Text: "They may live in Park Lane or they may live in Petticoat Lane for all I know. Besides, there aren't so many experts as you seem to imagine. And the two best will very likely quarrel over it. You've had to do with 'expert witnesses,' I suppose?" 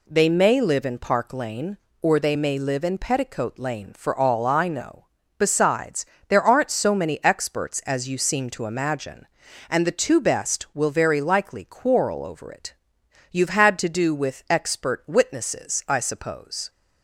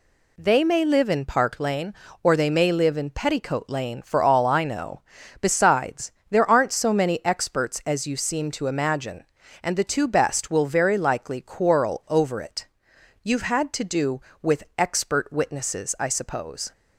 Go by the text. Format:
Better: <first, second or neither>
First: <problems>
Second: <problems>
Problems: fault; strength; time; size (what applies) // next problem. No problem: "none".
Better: neither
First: none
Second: none